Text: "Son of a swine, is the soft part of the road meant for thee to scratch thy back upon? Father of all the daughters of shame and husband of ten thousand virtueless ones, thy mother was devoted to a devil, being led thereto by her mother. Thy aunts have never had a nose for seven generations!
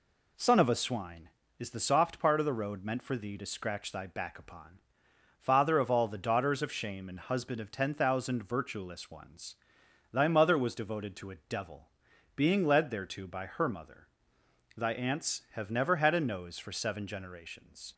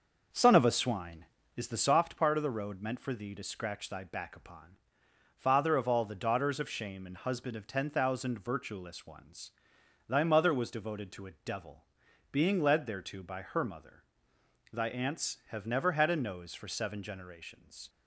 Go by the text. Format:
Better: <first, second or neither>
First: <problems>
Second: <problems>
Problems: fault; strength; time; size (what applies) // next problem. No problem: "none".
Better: first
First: none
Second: starts louder than the rest; until 2.1 s; 6 dB